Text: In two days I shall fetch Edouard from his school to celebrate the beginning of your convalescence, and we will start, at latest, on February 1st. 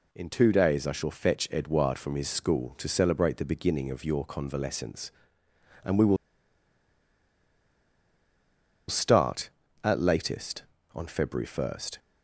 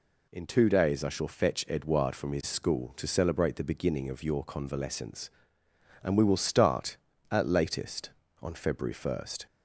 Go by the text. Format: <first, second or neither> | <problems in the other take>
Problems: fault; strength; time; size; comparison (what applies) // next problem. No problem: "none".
second | pauses between "will" and "start"; strong; at 6.1 s; 2.7 s long